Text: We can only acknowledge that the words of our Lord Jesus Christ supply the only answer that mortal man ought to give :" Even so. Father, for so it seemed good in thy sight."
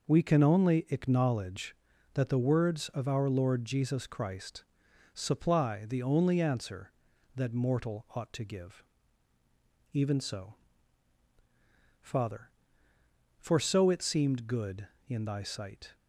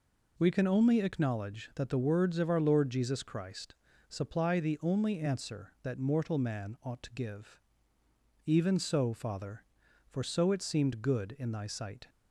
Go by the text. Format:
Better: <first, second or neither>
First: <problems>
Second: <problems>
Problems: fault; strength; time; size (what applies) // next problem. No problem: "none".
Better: second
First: pauses between "Christ" and "supply"; noticeable; at 4.6 s; 0.50 s long // skips "man"; at 8.0 s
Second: pauses between "Christ" and "supply"; slight; at 3.7 s; 0.34 s long